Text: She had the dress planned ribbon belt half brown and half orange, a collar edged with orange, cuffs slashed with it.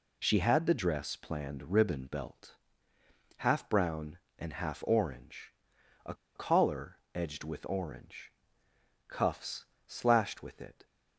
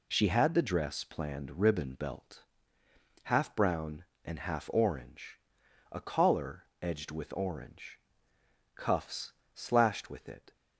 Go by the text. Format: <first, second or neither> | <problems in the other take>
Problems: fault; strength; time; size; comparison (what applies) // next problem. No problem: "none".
second | pauses between "belt" and "half"; noticeable; at 2.5 s; 0.84 s long; noticeable in the second // pauses between "a" and "collar"; slight; at 6.1 s; 0.20 s long // pauses between "collar" and "edged"; slight; at 6.9 s; 0.16 s long; slight in the second // pauses between "cuffs" and "slashed"; slight; at 9.6 s; 0.20 s long; slight in the second